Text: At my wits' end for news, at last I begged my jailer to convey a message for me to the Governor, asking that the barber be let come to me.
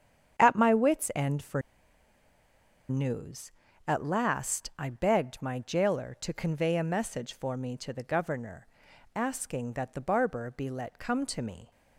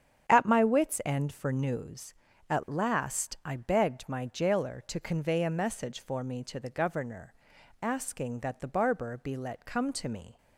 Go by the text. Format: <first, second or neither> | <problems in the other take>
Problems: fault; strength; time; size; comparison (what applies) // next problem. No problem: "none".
second | starts louder than the rest; strong; until 1.4 s; 8.5 dB; strong in the second // pauses between "for" and "news"; strong; at 1.6 s; 1.2 s long